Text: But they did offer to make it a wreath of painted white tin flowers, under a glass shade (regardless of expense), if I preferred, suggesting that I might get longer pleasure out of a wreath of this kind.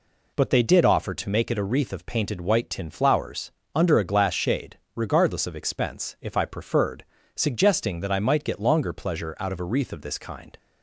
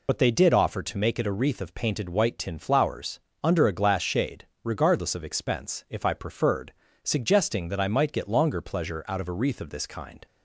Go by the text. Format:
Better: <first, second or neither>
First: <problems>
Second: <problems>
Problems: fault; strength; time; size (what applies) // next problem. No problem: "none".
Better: first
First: none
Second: loses the start of "But"; at 0.0 s; 55 ms